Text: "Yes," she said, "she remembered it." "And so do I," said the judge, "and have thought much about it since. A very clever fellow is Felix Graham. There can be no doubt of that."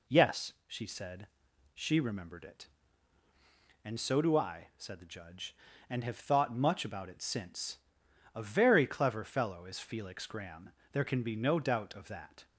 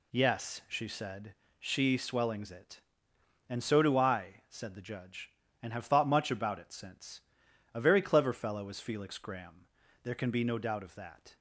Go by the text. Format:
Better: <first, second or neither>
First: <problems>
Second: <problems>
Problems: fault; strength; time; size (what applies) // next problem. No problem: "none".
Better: first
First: none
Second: says "swellings" for "remembered"; at 1.9 s